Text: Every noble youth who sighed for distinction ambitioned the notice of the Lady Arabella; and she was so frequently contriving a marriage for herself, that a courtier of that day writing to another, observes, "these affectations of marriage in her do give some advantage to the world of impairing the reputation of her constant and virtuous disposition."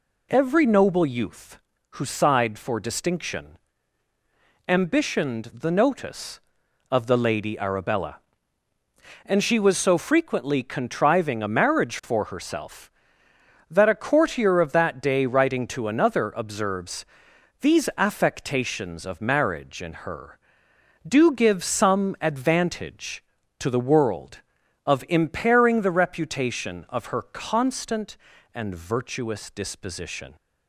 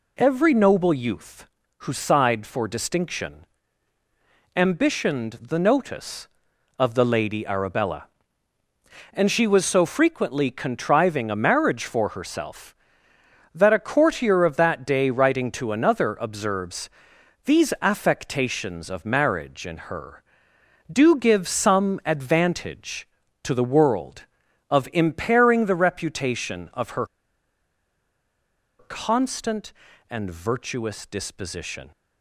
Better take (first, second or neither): first